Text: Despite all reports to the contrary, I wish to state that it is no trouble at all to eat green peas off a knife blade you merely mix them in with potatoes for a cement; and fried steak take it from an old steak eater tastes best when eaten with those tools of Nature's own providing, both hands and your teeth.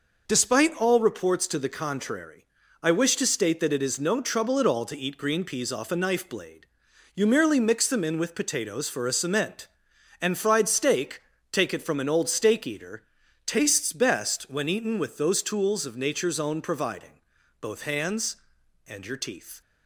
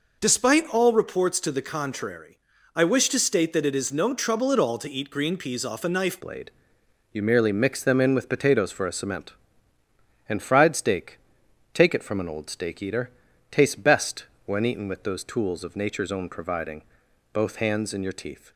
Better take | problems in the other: first | changes voice at "blade"; from 6.2 s on; 12.3 s long // pauses between "blade" and "you"; noticeable; at 6.5 s; 0.60 s long; noticeable in the first // pauses between "steak" and "take"; noticeable; at 11.1 s; 0.56 s long; slight in the first // pauses between "eater" and "tastes"; at 13.0 s; 0.42 s long; also in the first // pauses between "best" and "when"; slight; at 14.2 s; 0.20 s long

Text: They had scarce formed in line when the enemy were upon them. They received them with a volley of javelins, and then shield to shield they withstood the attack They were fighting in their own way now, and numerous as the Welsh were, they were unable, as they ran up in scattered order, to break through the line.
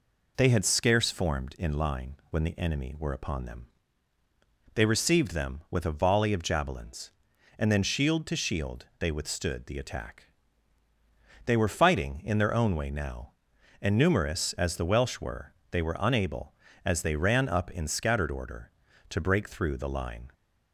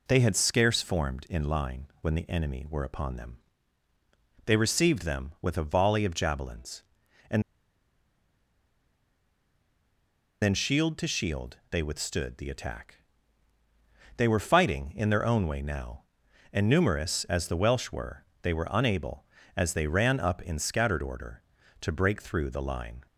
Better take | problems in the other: first | pauses between "and" and "then"; strong; at 7.4 s; 3.0 s long // pauses between "attack" and "They"; at 12.9 s; 1.2 s long; also in the first

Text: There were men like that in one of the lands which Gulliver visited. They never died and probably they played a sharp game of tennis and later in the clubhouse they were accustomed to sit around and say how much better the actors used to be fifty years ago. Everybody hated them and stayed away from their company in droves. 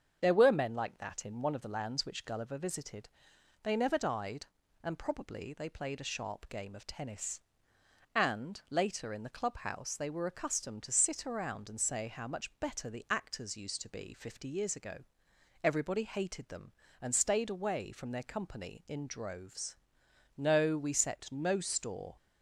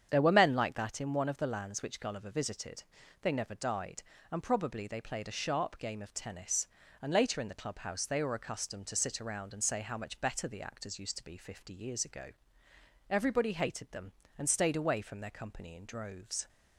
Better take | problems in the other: second | starts louder than the rest; strong; until 1.2 s; 7 dB; strong in the second // goes on to say "No we set no store"; strong; from 20.3 s on; 1.7 s long

